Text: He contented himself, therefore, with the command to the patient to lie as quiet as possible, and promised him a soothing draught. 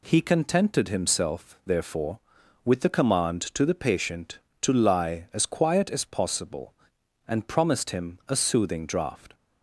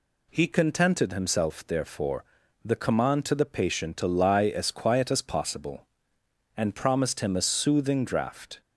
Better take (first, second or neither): first